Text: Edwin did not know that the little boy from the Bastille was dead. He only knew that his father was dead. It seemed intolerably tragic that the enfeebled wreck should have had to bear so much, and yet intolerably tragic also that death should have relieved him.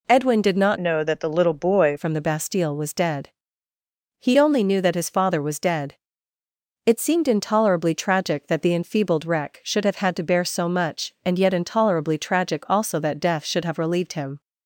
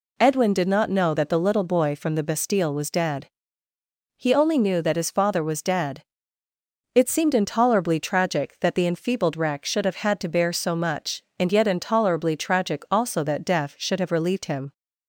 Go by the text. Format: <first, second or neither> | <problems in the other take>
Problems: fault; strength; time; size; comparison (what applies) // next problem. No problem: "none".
second | changes voice from "know" to "boy"; from 0.7 to 1.9 s; 1.2 s long